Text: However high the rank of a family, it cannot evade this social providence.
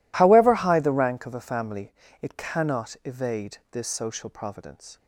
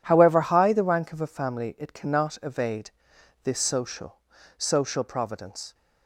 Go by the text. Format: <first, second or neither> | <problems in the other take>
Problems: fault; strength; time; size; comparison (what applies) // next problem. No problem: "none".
first | pauses between "evade" and "this"; noticeable; at 2.8 s; 0.54 s long; slight in the first // says "social" twice; at 4.5 s